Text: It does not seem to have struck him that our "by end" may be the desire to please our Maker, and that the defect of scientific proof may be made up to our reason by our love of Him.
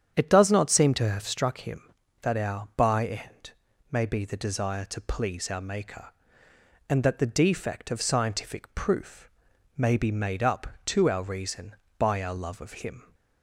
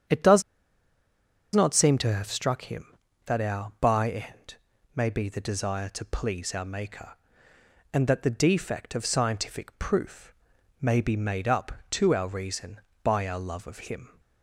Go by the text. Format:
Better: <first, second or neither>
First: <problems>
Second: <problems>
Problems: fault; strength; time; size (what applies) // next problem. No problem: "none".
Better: first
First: starts louder than the rest; strong; until 1.1 s; 9 dB // pauses between "end" and "may"; at 3.4 s; 0.40 s long // pauses between "proof" and "may"; noticeable; at 9.2 s; 0.48 s long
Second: starts louder than the rest; strong; until 2.2 s; 9 dB // pauses between "does" and "not"; at 0.4 s; 1.1 s long // pauses between "end" and "may"; at 4.5 s; 0.40 s long // pauses between "proof" and "may"; noticeable; at 10.3 s; 0.48 s long